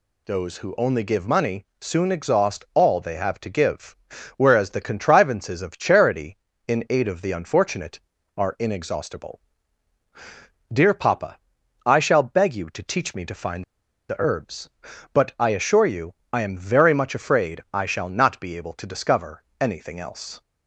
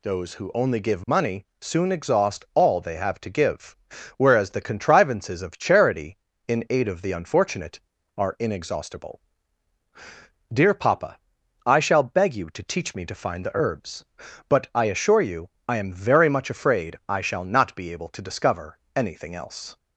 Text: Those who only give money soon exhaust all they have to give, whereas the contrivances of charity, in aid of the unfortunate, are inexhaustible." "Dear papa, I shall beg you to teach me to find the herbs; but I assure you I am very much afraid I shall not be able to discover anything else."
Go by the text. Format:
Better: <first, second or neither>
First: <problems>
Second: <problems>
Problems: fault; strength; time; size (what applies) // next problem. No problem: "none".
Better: second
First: pauses between "find" and "the"; at 13.6 s; 0.45 s long // pauses between "you" and "I"; slight; at 16.1 s; 0.18 s long // pauses between "discover" and "anything"; slight; at 19.4 s; 0.16 s long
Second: pauses between "you" and "I"; slight; at 15.5 s; 0.18 s long // pauses between "discover" and "anything"; slight; at 18.7 s; 0.16 s long